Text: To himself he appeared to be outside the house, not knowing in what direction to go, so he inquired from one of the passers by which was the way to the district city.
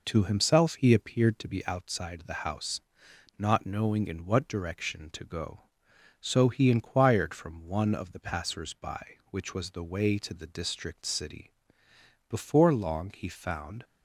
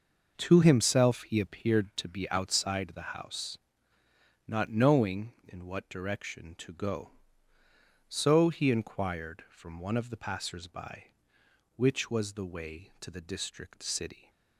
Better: second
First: goes on to say "Before long he found"; from 12.2 s on; 1.5 s long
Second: none

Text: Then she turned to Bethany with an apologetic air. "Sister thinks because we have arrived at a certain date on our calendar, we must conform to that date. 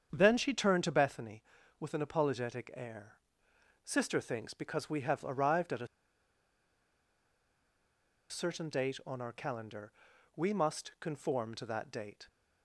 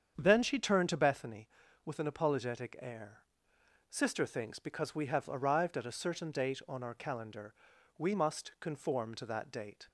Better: second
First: starts louder than the rest; strong; until 1.1 s; 8 dB // pauses between "a" and "certain"; strong; at 5.8 s; 2.4 s long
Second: starts louder than the rest; strong; until 1.2 s; 8 dB

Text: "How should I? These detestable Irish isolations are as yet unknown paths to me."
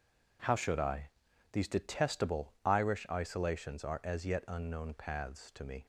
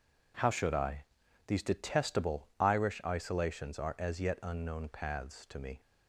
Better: neither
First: none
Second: none

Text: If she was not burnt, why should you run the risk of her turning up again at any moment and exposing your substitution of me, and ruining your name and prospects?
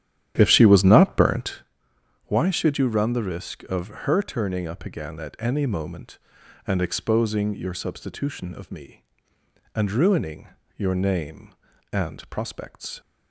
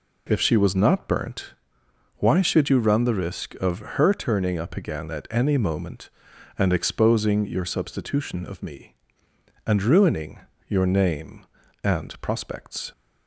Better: second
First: starts louder than the rest; strong; until 1.7 s; 11 dB // pauses between "ruining" and "your"; slight; at 10.4 s; 0.28 s long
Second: pauses between "ruining" and "your"; slight; at 10.3 s; 0.28 s long

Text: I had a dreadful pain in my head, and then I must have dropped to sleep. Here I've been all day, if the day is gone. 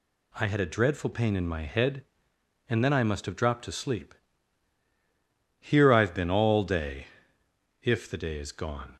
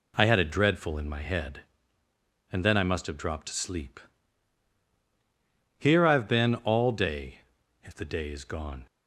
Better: first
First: none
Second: skips "pain"; at 0.9 s

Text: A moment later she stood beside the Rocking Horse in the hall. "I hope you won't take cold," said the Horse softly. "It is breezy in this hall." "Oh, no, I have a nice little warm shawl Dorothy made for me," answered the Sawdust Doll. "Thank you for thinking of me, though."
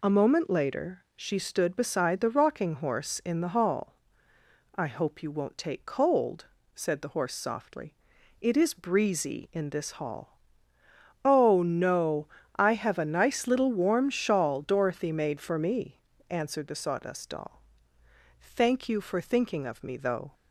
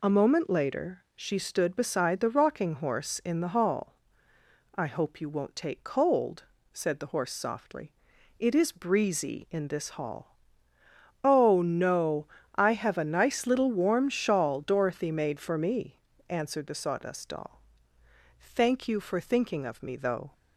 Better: neither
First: none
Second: none

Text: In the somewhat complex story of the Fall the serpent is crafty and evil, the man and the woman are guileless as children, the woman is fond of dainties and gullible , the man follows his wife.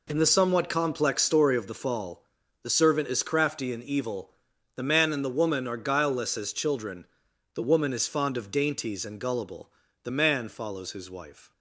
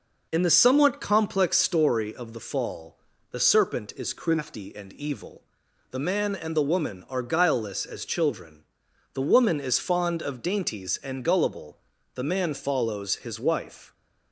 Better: second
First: pauses between "Fall" and "the"; at 2.2 s; 0.38 s long // says "servant" for "serpent"; at 2.7 s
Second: pauses between "Fall" and "the"; slight; at 2.9 s; 0.34 s long

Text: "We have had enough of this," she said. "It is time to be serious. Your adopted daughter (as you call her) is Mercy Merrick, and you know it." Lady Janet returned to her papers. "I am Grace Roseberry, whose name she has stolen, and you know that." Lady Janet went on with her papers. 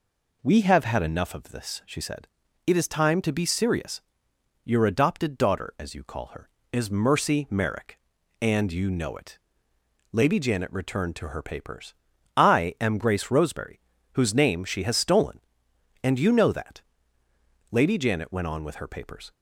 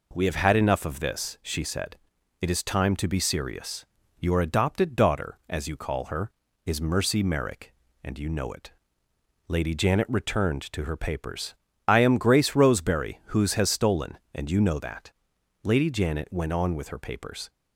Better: first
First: none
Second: skips "name she"; at 13.5 s

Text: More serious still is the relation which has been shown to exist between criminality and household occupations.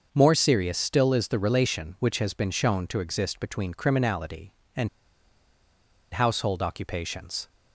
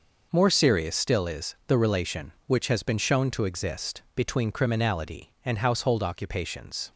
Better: second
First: starts louder than the rest; until 1.1 s; 6 dB // pauses between "and" and "household"; at 4.8 s; 1.2 s long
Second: none

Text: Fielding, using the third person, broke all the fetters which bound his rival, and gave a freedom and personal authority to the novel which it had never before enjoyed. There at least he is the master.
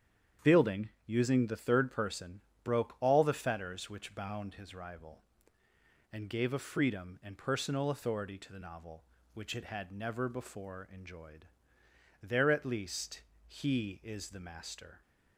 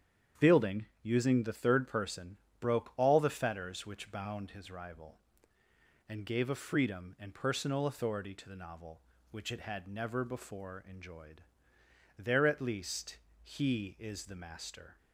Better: neither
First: starts louder than the rest; strong; until 1.5 s; 8.5 dB // pauses between "least" and "he"; slight; at 13.2 s; 0.26 s long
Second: starts louder than the rest; strong; until 1.5 s; 8.5 dB // pauses between "least" and "he"; slight; at 13.1 s; 0.26 s long

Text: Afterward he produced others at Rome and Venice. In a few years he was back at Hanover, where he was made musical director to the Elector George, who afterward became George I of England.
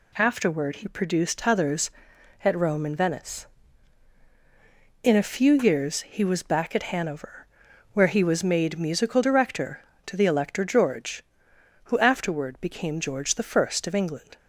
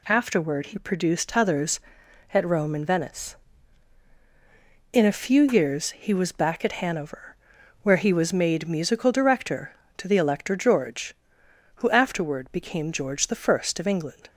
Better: neither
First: none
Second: none

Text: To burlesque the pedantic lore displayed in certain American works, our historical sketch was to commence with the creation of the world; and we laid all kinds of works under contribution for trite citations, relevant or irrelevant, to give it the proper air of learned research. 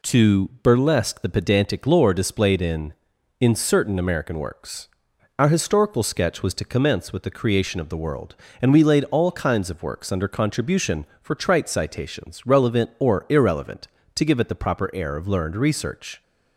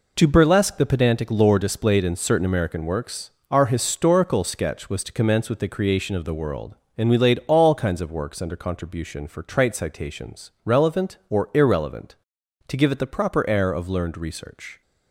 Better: second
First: says "in" twice; at 3.3 s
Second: none

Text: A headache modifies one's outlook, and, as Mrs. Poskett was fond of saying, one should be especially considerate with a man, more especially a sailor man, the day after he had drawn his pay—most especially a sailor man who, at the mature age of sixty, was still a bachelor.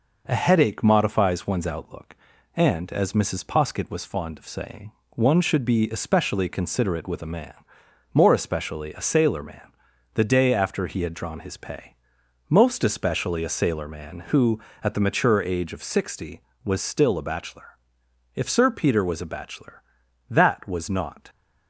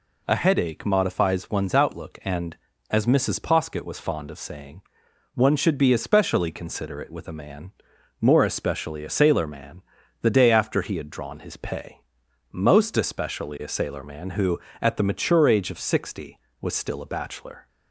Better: second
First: goes on to say "If Sir Peter was a bachelor that was not"; strong; from 18.3 s on; 2.9 s long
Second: none

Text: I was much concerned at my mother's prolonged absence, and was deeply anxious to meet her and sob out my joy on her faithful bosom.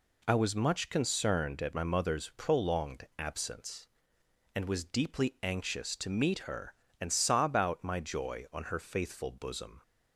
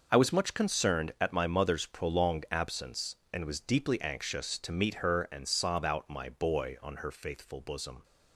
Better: first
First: none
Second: says "boy" for "joy"; at 6.2 s

